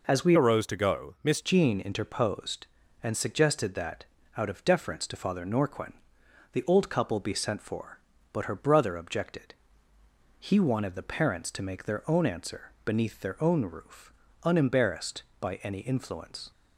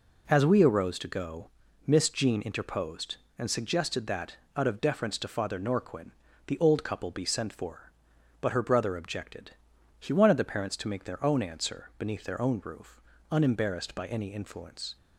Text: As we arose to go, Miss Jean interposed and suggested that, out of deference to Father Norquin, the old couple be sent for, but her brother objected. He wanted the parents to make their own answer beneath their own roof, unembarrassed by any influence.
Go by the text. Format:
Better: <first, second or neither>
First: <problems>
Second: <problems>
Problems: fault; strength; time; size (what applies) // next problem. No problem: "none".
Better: second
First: changes voice from "arose" to "Miss"; from 0.3 to 1.4 s; 1.1 s long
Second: none